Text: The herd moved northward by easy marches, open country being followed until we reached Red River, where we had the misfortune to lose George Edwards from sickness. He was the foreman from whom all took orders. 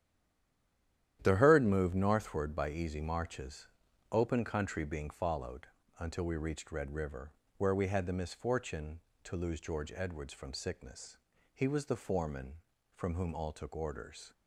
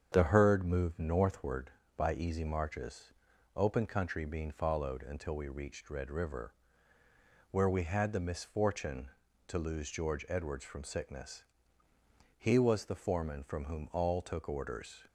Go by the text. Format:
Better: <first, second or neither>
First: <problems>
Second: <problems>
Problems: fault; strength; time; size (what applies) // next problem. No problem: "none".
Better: second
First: stays silent before the first word; noticeable; until 1.2 s; 1.2 s long // starts louder than the rest; strong; until 2.2 s; 11 dB // pauses between "followed" and "until"; slight; at 5.6 s; 0.32 s long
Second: starts louder than the rest; strong; until 1.1 s; 7.5 dB